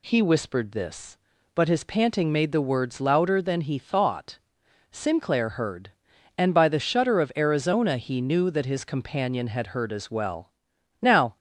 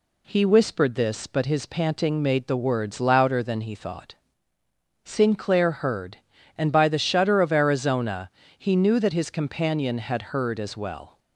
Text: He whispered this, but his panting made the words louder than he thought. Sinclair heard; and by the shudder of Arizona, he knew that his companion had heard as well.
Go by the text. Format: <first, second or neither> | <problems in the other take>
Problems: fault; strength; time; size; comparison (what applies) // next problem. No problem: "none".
second | goes on to say "Now"; slight; from 11.0 s on; 0.36 s long